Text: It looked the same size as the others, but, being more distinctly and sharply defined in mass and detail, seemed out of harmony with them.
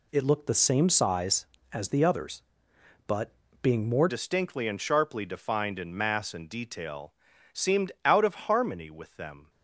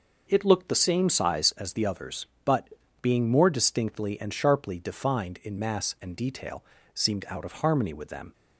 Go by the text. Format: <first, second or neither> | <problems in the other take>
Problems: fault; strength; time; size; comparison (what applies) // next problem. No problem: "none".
second | changes voice at "distinctly"; from 4.0 s on; 5.4 s long // pauses between "seemed" and "out"; slight; at 7.8 s; 0.16 s long